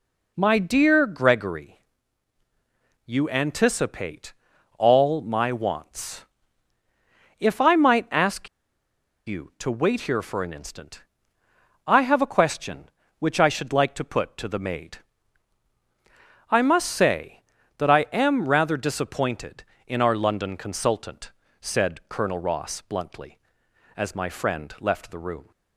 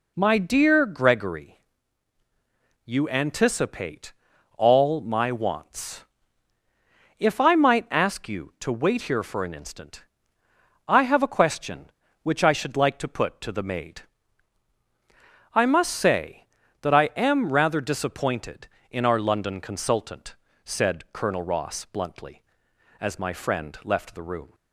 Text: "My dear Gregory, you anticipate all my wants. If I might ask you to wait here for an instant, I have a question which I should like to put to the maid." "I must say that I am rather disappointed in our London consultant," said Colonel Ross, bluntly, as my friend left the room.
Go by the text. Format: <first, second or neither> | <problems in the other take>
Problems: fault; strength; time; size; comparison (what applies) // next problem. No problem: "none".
second | pauses between "anticipate" and "all"; noticeable; at 4.3 s; 0.46 s long; noticeable in the second // pauses between "ask" and "you"; noticeable; at 8.4 s; 0.78 s long